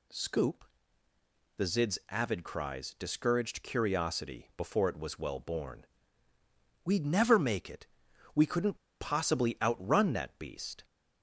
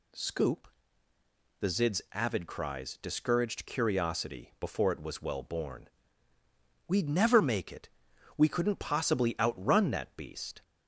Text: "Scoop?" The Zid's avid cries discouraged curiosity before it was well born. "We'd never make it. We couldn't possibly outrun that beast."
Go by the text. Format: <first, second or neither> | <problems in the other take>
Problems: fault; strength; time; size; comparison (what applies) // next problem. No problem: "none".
second | pauses between "couldn't" and "possibly"; slight; at 8.7 s; 0.22 s long